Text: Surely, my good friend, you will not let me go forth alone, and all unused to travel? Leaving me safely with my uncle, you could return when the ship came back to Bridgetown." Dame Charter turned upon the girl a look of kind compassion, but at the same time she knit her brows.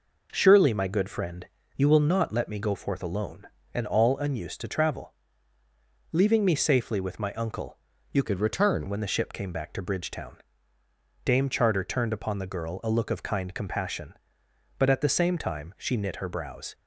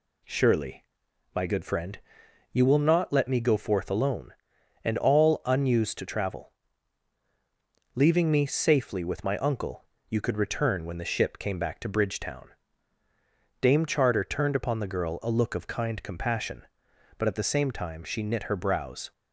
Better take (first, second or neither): second